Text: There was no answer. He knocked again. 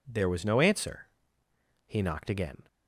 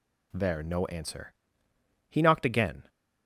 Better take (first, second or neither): first